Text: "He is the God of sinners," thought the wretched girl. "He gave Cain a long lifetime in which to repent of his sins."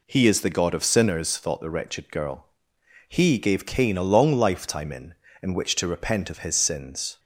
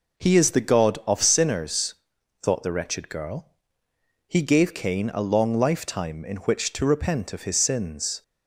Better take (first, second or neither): second